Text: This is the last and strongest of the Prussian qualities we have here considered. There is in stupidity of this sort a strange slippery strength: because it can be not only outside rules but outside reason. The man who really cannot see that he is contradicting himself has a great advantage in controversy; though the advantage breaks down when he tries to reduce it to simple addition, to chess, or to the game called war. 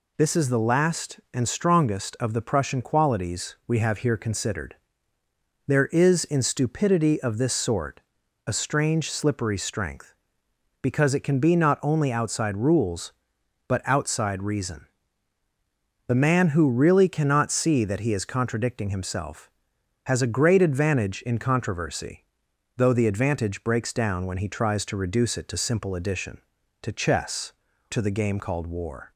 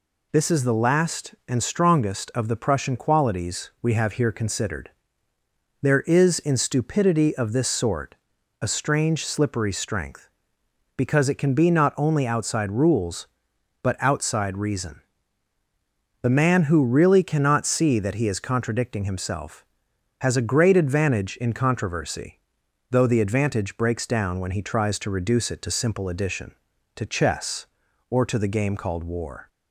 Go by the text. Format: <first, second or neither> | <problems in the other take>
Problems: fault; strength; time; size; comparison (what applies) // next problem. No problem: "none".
second | pauses between "sort" and "a"; noticeable; at 7.9 s; 0.48 s long; noticeable in the second // skips "or"; at 27.7 s